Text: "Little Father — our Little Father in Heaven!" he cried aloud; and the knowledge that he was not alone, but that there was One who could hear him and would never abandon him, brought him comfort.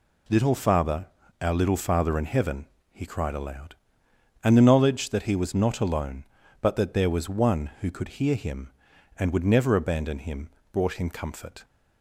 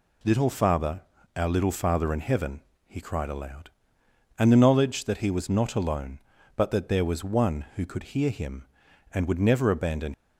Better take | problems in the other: first | stops before "him brought him comfort"; at 10.1 s

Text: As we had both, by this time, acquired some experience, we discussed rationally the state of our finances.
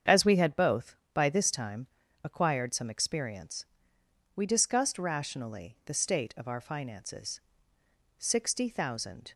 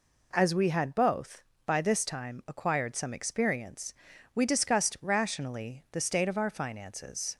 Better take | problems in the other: second | starts louder than the rest; strong; until 1.2 s; 7.5 dB // goes on to say "Sixty thousand"; noticeable; from 8.1 s on; 1.1 s long

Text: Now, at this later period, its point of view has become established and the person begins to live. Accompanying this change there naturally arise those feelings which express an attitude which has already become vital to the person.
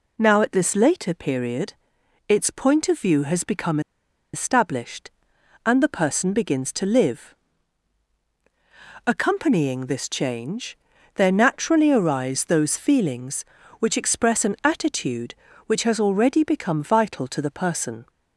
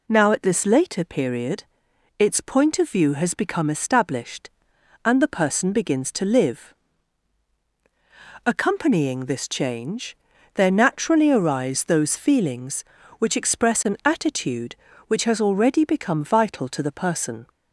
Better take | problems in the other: second | pauses between "become" and "established"; noticeable; at 3.8 s; 0.53 s long // pauses between "change" and "there"; at 10.7 s; 0.38 s long; also in the second

